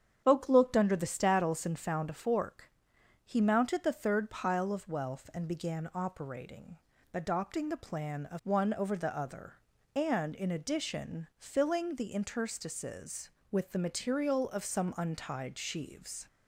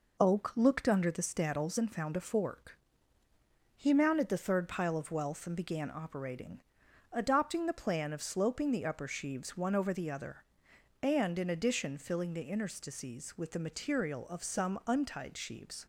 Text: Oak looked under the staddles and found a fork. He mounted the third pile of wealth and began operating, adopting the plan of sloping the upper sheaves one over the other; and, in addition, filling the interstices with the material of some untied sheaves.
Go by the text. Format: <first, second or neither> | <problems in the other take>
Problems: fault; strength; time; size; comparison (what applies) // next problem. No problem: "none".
second | starts louder than the rest; strong; until 1.2 s; 8 dB // skips "sloping the upper sheaves"; at 8.4 s